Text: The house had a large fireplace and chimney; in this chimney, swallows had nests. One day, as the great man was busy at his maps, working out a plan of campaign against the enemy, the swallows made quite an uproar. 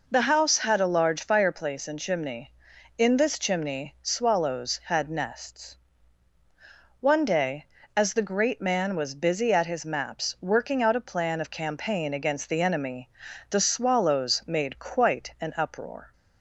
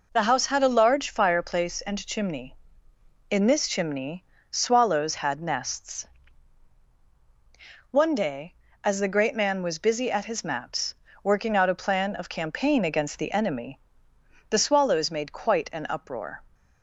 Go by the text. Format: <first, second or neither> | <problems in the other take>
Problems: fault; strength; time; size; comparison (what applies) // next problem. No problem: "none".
neither | none